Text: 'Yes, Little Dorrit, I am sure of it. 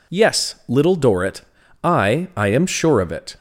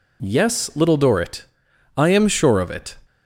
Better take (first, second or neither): second